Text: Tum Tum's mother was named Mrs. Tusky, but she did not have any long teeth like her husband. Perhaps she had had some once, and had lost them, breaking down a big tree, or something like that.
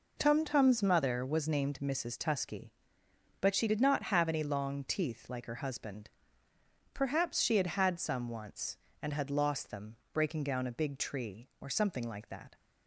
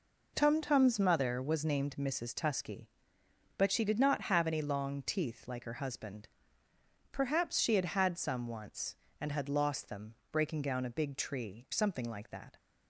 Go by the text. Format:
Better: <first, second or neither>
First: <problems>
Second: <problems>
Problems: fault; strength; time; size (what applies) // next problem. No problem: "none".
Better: first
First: none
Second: skips "or"; at 11.6 s